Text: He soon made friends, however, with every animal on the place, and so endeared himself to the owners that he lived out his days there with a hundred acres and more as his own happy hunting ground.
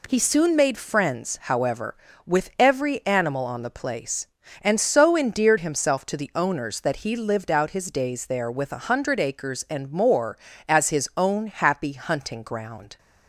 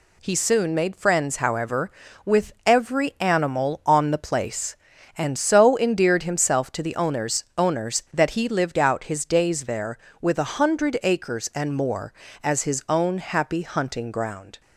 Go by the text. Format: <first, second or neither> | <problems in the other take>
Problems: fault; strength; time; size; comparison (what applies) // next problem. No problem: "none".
first | says "owners" twice; at 7.5 s